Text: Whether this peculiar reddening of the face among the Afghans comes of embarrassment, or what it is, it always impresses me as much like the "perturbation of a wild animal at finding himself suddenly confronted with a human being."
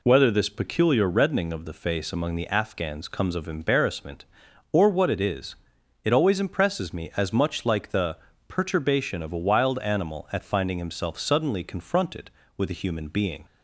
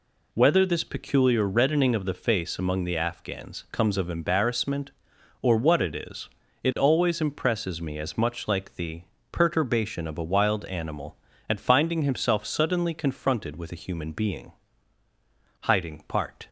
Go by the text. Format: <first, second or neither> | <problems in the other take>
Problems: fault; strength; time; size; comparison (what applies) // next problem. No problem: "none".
first | pauses between "the" and "perturbation"; slight; at 9.0 s; 0.28 s long; slight in the first // goes on to say "Hiding part"; noticeable; from 15.6 s on; 0.88 s long